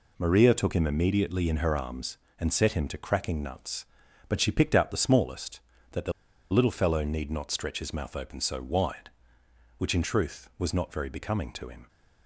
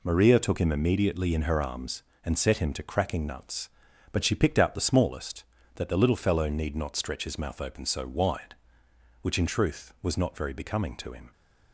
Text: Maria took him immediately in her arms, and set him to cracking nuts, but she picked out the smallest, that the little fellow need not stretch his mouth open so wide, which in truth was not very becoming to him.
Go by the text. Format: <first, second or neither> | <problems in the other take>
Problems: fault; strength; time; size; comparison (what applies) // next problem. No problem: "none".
second | pauses between "the" and "little"; at 6.1 s; 0.39 s long